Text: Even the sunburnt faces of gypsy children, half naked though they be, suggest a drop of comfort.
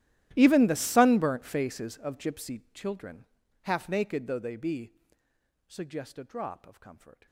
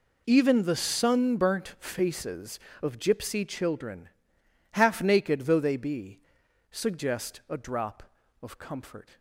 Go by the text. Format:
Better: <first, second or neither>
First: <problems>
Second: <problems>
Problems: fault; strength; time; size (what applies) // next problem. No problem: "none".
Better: second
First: gets quieter; strong; throughout; 24.5 dB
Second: none